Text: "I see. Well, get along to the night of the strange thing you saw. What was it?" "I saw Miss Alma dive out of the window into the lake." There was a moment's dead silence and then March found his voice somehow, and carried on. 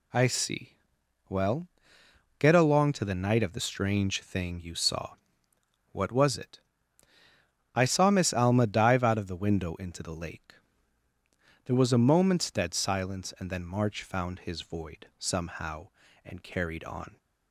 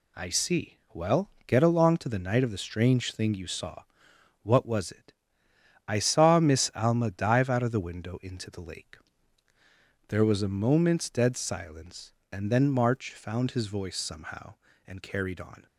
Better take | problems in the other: second | says "void" for "voice"; at 14.6 s

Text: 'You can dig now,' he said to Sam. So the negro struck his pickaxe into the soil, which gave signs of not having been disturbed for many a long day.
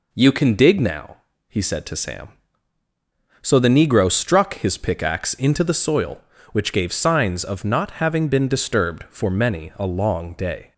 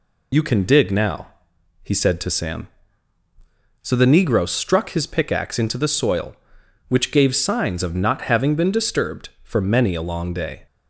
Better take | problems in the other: first | loses the start of "You"; at 0.3 s; 45 ms

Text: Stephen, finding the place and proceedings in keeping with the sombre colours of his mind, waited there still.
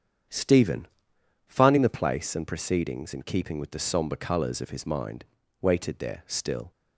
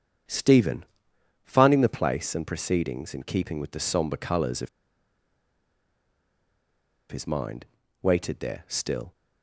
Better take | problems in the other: first | starts louder than the rest; strong; until 1.8 s; 8 dB; strong in the first // pauses between "of" and "his"; strong; at 4.6 s; 2.4 s long

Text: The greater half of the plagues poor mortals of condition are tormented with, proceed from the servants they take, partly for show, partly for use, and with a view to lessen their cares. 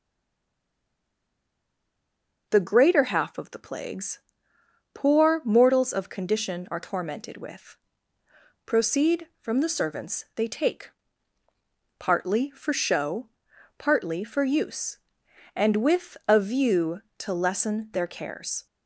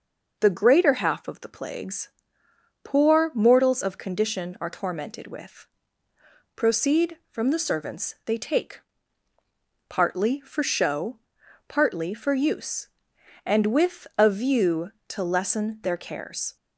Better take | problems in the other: second | stays silent before the first word; until 2.4 s; 2.4 s long // pauses between "plagues" and "poor"; noticeable; at 4.1 s; 0.74 s long; noticeable in the second

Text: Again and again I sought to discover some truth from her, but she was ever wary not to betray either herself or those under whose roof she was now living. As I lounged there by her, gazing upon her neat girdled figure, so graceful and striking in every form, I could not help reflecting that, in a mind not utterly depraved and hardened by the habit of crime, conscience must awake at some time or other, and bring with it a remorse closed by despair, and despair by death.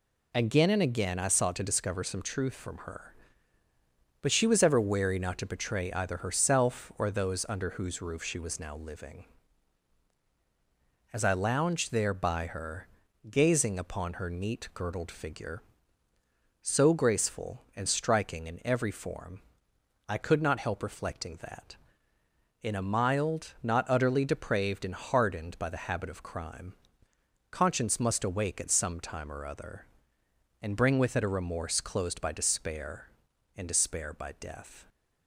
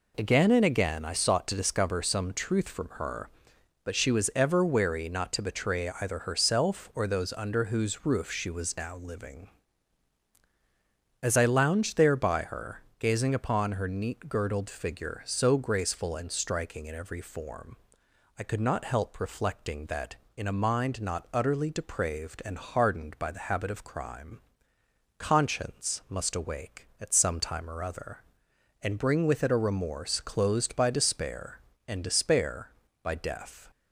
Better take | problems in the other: second | says "mild" for "mind"; at 22.8 s

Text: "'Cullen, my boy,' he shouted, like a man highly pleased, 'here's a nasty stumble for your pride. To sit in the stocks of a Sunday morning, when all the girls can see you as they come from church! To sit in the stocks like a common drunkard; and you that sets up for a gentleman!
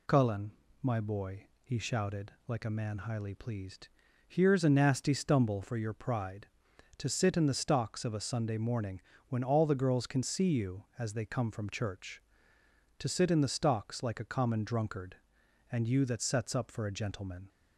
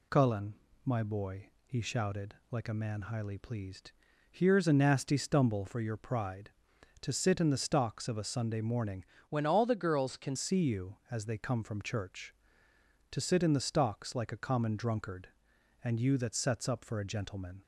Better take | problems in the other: first | changes voice from "when" to "can"; from 9.2 to 10.3 s; 1.1 s long

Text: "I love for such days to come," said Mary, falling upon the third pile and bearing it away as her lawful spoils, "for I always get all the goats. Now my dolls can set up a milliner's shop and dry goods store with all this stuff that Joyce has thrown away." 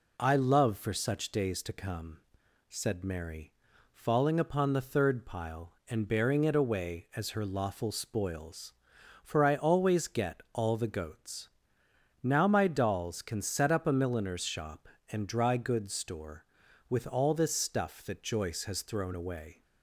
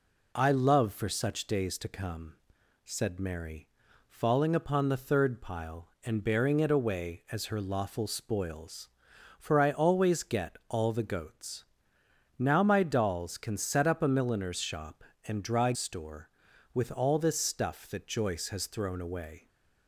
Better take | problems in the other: first | skips "goods"; at 15.7 s

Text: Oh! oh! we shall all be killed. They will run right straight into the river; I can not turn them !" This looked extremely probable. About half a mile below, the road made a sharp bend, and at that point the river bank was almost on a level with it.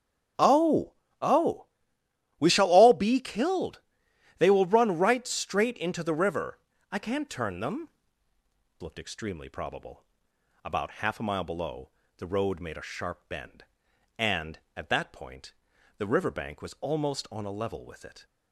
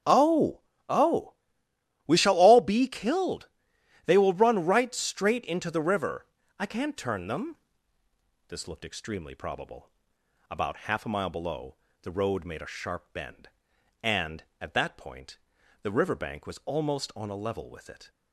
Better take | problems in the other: second | starts louder than the rest; strong; until 1.6 s; 8 dB; strong in the second // skips "This"; at 8.8 s // pauses between "point" and "the"; noticeable; at 15.5 s; 0.46 s long; noticeable in the second

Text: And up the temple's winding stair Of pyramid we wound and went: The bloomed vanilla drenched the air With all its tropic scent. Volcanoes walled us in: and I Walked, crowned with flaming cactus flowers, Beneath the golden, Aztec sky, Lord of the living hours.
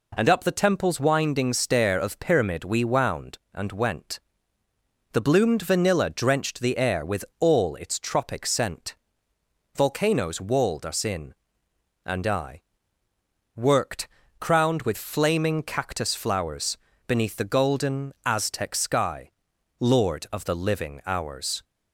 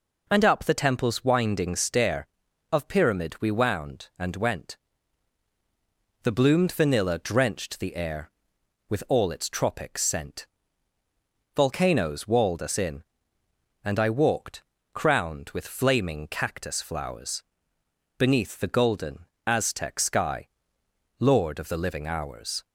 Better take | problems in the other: second | says "Worked" for "Walked"; at 13.5 s

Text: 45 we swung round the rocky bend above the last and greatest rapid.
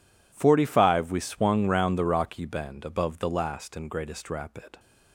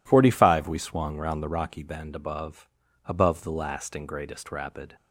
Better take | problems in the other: first | says "above" twice; at 3.0 s

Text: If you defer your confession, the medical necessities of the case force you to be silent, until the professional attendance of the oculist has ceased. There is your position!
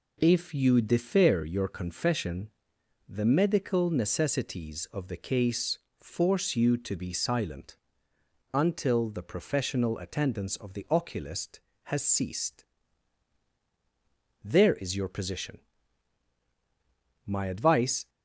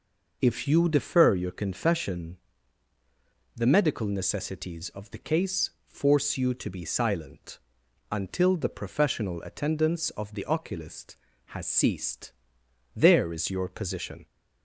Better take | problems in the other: second | pauses between "case" and "force"; slight; at 5.7 s; 0.22 s long; slight in the second // goes on to say "My advice"; noticeable; from 17.2 s on; 0.84 s long

